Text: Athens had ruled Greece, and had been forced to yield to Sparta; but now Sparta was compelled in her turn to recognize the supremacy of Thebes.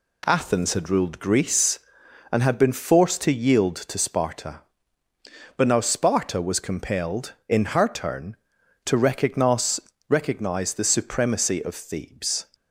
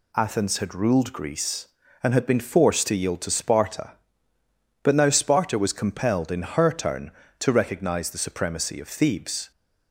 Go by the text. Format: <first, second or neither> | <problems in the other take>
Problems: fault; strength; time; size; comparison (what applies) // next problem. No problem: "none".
second | says "recognize" twice; at 10.0 s